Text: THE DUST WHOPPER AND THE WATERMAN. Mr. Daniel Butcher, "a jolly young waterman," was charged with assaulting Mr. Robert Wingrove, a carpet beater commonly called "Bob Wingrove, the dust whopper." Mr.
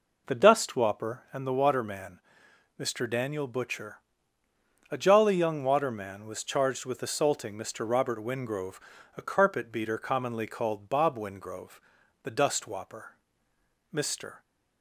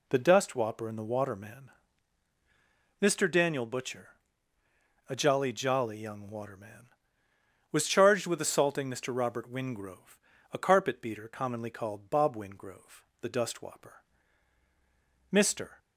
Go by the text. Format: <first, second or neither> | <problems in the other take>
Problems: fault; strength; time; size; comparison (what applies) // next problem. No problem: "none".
first | says "jolly" twice; at 5.5 s